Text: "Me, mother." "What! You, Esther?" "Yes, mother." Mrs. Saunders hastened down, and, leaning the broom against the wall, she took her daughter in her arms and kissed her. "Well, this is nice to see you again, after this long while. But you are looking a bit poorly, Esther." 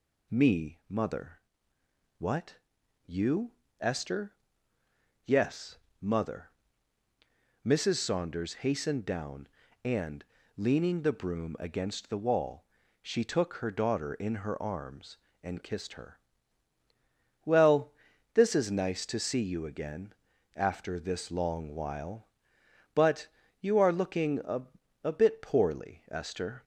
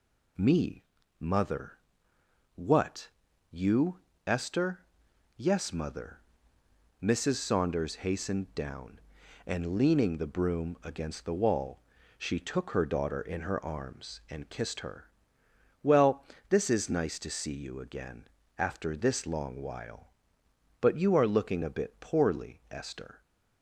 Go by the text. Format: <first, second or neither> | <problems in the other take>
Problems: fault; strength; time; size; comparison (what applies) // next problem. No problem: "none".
second | pauses between "But" and "you"; slight; at 23.2 s; 0.32 s long // says "a" twice; at 25.0 s